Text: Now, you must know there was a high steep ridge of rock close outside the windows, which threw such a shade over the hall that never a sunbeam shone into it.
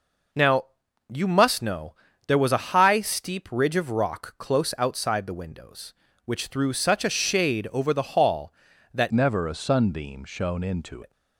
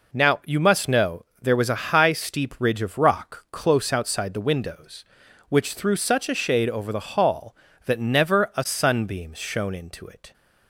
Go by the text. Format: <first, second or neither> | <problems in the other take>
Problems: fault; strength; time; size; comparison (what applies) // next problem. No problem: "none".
second | pauses between "know" and "there"; slight; at 1.9 s; 0.34 s long; slight in the second // changes voice from "never" to "into"; from 9.1 to 11.0 s; 1.9 s long